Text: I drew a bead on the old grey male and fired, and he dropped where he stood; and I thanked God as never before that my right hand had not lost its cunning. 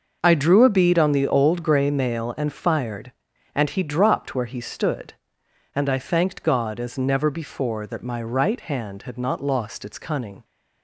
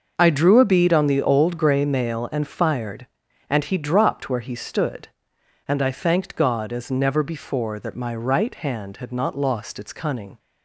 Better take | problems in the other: neither | starts louder than the rest; the same in both

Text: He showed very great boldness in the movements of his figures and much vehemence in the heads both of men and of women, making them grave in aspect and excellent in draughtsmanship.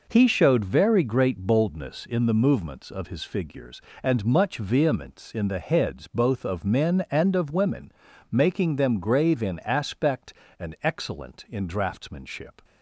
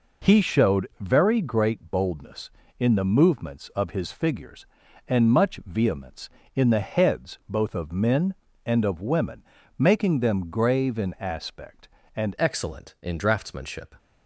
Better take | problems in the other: first | changes voice at "excellent"; from 12.3 s on; 1.6 s long

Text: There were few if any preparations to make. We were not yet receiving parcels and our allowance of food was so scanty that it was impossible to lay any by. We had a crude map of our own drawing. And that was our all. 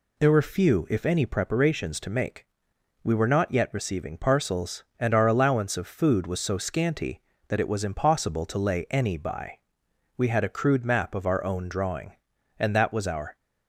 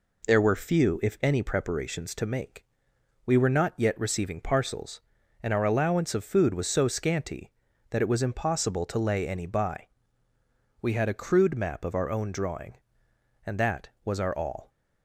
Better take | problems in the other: second | stops before "all"; at 13.3 s

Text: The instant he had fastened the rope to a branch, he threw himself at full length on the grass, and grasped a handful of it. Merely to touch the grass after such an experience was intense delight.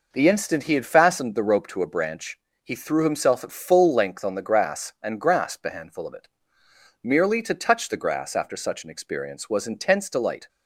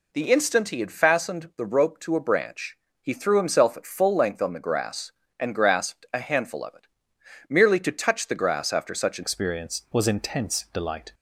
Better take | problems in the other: first | changes voice at "experience"; from 9.2 s on; 1.9 s long

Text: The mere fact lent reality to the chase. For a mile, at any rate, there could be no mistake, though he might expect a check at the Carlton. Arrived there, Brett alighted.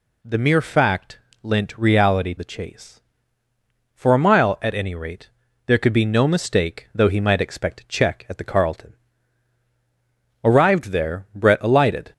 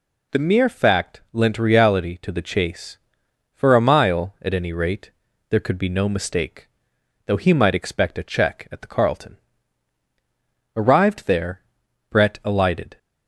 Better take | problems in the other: second | pauses between "fact" and "lent"; slight; at 1.1 s; 0.24 s long // skips "to"; at 2.3 s

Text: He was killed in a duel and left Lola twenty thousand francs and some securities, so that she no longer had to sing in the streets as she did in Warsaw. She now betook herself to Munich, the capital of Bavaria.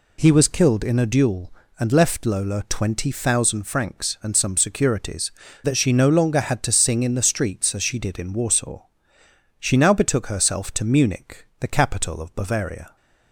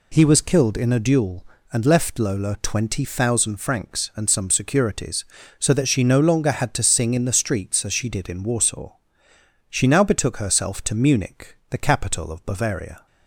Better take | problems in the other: second | skips "so"; at 5.4 s

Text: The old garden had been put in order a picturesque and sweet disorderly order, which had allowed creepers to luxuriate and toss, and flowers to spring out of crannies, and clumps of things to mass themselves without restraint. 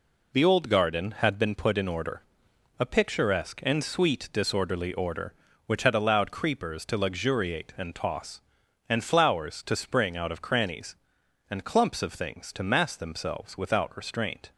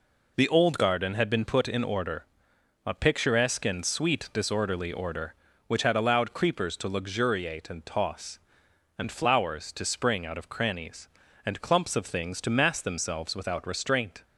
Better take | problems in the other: neither | pauses between "order" and "a"; noticeable; the same in both

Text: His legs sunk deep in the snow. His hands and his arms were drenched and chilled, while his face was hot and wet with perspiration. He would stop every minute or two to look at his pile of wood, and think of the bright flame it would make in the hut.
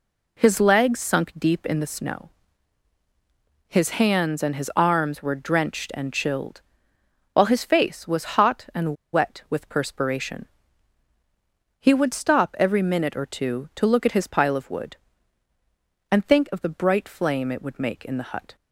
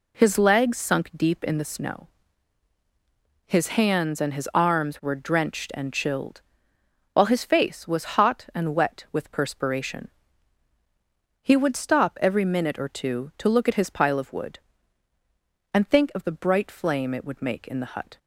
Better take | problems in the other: second | pauses between "and" and "wet"; slight; at 8.9 s; 0.19 s long

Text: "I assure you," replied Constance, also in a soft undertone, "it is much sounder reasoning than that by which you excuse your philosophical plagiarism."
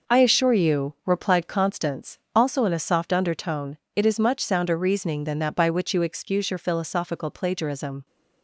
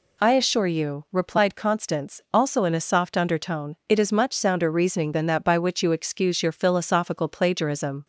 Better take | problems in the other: second | gets quieter; strong; throughout; 8 dB

